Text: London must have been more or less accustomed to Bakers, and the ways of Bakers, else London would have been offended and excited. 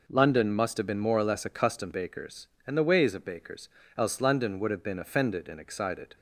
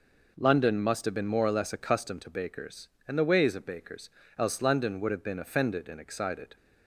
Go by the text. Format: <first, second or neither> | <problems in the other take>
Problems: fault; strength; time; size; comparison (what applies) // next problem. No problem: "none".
second | skips "to"; at 1.9 s